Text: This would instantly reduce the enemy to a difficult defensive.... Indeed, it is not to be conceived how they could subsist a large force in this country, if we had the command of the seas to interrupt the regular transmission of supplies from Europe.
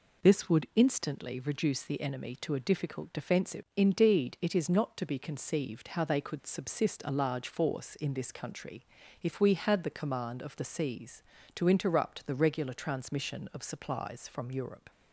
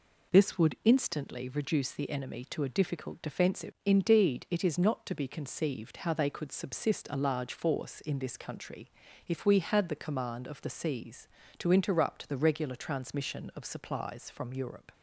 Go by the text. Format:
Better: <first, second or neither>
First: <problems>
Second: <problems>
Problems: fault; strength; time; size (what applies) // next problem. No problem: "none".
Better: neither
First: none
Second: none